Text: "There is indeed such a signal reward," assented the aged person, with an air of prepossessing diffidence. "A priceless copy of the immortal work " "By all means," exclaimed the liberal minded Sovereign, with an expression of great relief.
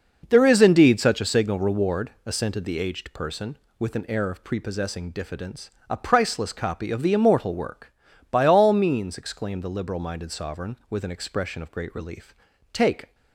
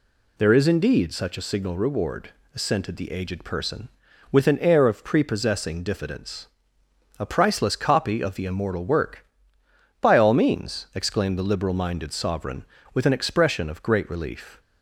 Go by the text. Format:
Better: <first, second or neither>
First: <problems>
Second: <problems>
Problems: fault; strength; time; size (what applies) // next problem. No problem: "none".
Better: second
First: goes on to say "Take"; slight; from 12.7 s on; 0.42 s long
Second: none